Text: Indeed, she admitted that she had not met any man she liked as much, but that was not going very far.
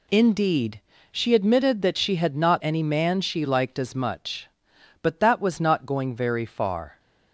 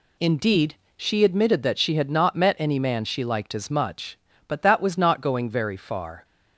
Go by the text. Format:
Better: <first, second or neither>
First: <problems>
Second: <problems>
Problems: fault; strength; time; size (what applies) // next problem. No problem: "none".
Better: second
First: skips "met"; at 2.6 s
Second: none